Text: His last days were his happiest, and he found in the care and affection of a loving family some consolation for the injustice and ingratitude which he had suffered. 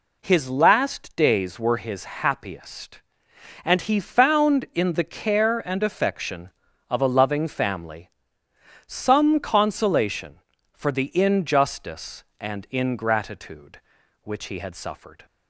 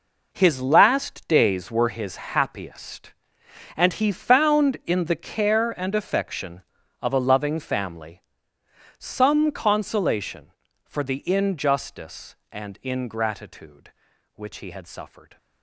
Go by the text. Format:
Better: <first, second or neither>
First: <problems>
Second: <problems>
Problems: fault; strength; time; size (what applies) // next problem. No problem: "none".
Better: first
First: pauses between "family" and "some"; noticeable; at 8.0 s; 0.76 s long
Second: gets quieter; strong; throughout; 11.5 dB // pauses between "family" and "some"; noticeable; at 8.2 s; 0.76 s long